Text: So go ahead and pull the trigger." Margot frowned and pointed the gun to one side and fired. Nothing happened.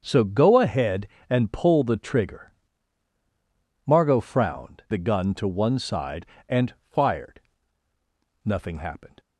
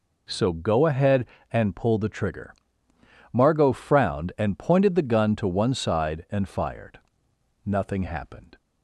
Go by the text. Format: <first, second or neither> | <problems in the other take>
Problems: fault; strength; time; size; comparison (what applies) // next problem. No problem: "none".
second | starts louder than the rest; until 1.0 s; 7 dB // skips "and pointed"; at 4.8 s // pauses between "and" and "fired"; slight; at 6.7 s; 0.18 s long